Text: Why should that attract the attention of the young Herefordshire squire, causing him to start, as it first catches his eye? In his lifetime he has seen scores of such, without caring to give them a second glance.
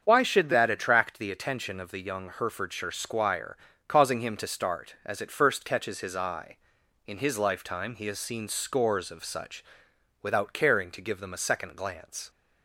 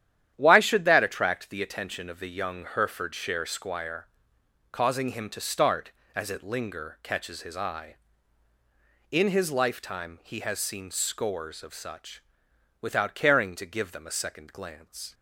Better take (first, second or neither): first